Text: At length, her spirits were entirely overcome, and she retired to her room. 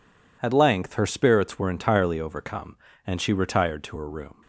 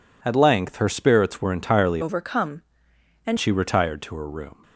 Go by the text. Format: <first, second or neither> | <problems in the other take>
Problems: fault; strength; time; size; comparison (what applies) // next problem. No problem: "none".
first | changes voice from "overcome" to "and"; from 2.0 to 3.3 s; 1.3 s long